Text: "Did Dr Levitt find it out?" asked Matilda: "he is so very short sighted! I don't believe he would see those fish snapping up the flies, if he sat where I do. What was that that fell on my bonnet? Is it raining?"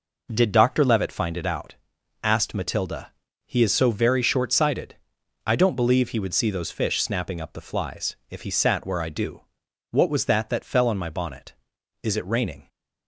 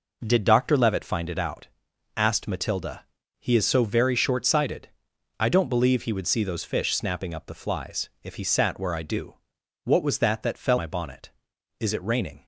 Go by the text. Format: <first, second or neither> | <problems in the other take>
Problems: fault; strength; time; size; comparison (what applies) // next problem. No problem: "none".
first | skips "on"; at 10.7 s